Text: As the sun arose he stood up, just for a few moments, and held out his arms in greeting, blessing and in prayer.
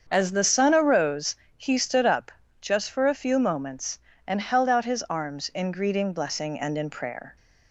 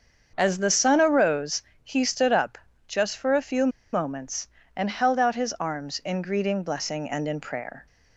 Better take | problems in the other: first | starts louder than the rest; until 1.3 s; 7 dB; also in the first // pauses between "arose" and "he"; slight; at 1.6 s; 0.22 s long; slight in the first // pauses between "few" and "moments"; slight; at 3.6 s; 0.24 s long

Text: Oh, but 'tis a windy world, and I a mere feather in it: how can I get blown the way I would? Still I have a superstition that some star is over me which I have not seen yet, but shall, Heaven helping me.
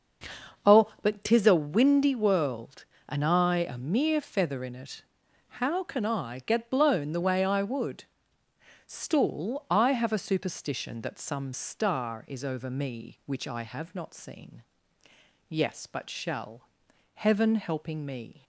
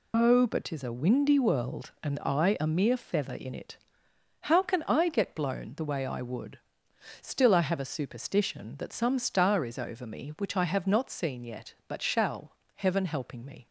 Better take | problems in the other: second | starts louder than the rest; noticeable; until 1.7 s; 6 dB // says "yes" for "yet"; at 15.4 s

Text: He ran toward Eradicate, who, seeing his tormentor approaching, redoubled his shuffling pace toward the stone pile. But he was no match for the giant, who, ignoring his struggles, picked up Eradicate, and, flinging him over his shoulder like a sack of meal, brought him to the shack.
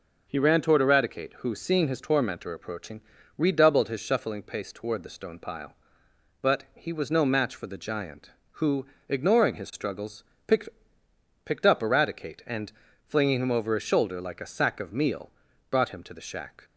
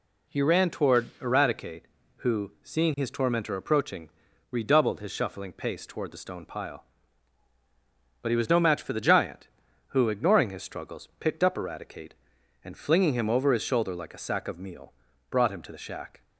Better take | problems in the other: second | says "picked" twice; at 11.4 s

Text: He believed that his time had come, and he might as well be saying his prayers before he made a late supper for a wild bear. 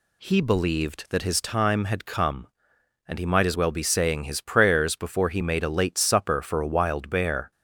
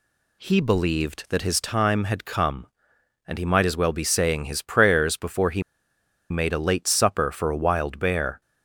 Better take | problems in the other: first | pauses between "he" and "made"; noticeable; at 5.6 s; 0.69 s long

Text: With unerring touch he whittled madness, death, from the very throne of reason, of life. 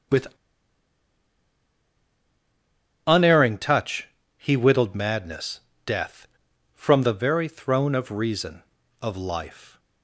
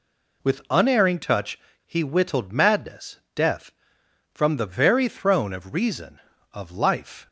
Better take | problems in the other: second | starts louder than the rest; strong; until 3.9 s; 8.5 dB // pauses between "With" and "unerring"; strong; at 0.2 s; 2.8 s long // pauses between "touch" and "he"; slight; at 4.0 s; 0.30 s long; slight in the second

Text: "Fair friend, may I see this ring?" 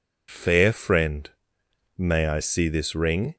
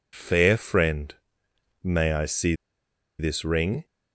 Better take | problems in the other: first | pauses between "see" and "this"; noticeable; at 2.5 s; 0.65 s long

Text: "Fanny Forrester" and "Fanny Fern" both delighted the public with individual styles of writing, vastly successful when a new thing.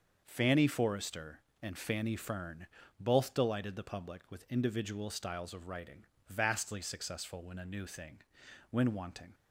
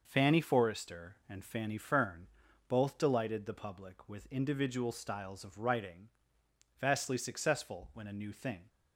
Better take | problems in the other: second | starts louder than the rest; until 1.2 s; 6.5 dB // pauses between "Fern" and "both"; slight; at 2.6 s; 0.32 s long; also in the second // goes on to say "When wanting"; noticeable; from 8.6 s on; 0.64 s long

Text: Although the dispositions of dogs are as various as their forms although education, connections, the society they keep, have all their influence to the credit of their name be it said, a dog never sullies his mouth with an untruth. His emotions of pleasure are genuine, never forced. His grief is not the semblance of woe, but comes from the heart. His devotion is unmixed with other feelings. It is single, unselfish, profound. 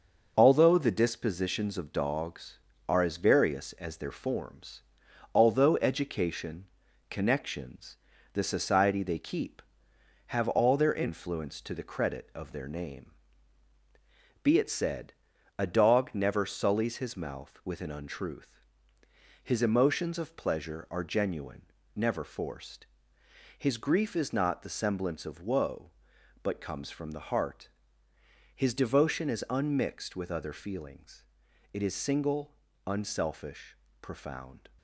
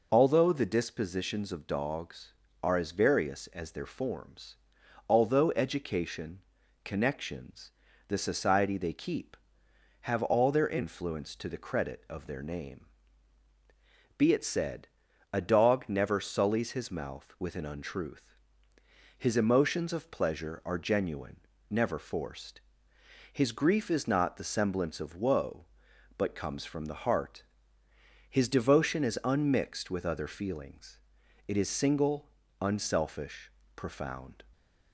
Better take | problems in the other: second | gets quieter; noticeable; throughout; 5.5 dB // pauses between "forms" and "although"; noticeable; at 4.8 s; 0.52 s long; noticeable in the second // pauses between "name" and "be"; strong; at 13.1 s; 1.3 s long; strong in the second

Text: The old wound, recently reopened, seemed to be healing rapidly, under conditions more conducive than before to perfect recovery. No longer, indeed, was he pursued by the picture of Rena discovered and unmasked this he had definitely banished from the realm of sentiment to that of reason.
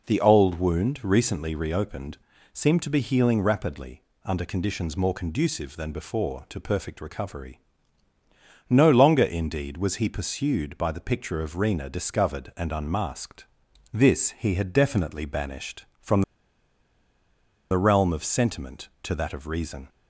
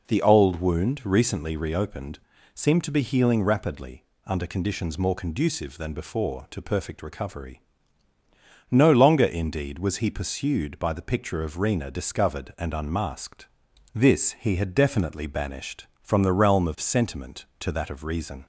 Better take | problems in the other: second | pauses between "unmasked" and "this"; noticeable; at 13.4 s; 0.50 s long; noticeable in the second // pauses between "from" and "the"; strong; at 16.2 s; 1.4 s long

